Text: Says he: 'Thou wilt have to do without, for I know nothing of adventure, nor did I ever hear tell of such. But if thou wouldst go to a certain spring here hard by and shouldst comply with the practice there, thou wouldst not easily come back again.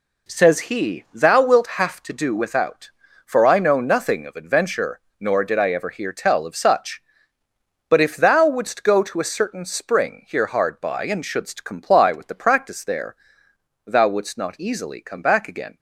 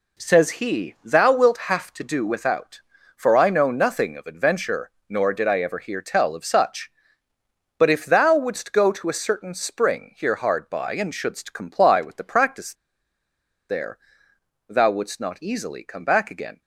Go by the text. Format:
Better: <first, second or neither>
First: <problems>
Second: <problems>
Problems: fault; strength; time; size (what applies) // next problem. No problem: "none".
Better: first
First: none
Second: pauses between "practice" and "there"; noticeable; at 12.7 s; 0.95 s long